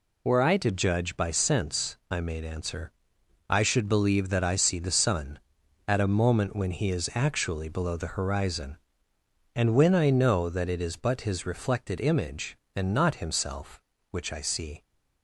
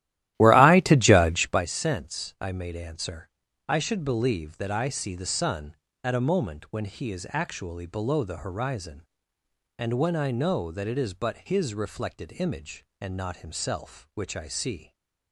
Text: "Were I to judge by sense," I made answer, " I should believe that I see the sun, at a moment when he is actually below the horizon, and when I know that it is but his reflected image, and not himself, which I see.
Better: first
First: none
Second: starts louder than the rest; strong; until 1.7 s; 13.5 dB

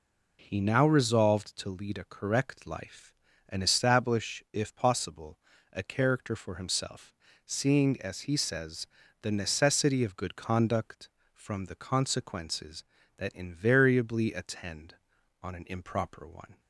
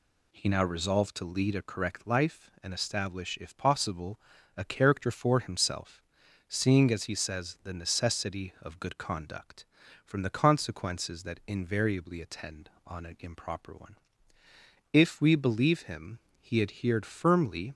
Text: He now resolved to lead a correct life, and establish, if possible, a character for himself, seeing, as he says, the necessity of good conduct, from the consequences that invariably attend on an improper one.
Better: first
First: none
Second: goes on to say "If we believe him he adhered firmly"; strong; from 14.9 s on; 2.8 s long

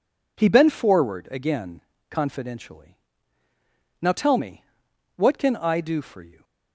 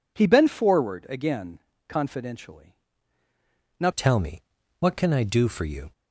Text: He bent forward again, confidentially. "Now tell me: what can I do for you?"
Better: first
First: none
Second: changes voice at "tell"; from 3.9 s on; 2.0 s long

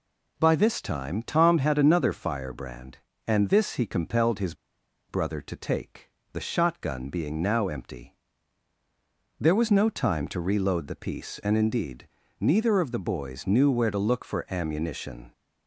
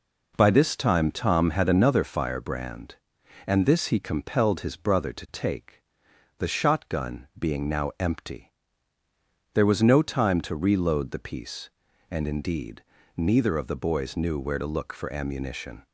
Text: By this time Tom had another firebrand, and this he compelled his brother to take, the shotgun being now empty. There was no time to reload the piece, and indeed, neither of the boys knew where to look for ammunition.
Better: second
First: pauses between "his" and "brother"; noticeable; at 4.5 s; 0.55 s long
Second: none

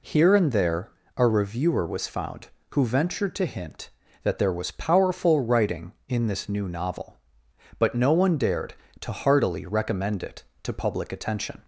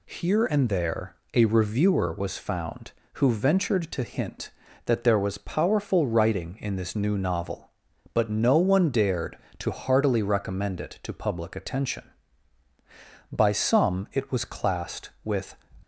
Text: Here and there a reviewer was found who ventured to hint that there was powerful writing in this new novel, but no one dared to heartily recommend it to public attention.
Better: first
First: pauses between "there" and "a"; slight; at 0.9 s; 0.24 s long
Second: pauses between "there" and "a"; slight; at 1.1 s; 0.18 s long // goes on to say "By some it was classed with"; strong; from 13.3 s on; 2.2 s long

